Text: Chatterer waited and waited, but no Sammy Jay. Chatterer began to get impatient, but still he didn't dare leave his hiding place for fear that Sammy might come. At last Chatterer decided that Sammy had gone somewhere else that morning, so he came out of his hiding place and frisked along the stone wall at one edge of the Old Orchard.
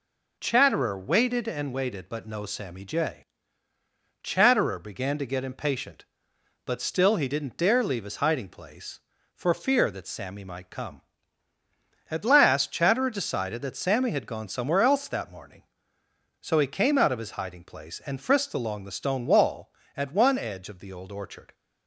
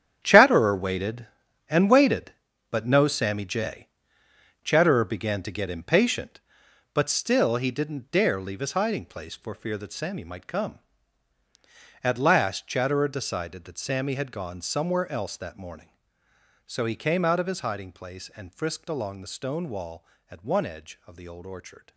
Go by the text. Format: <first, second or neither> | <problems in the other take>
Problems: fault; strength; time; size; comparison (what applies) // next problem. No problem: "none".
first | gets quieter; strong; throughout; 12.5 dB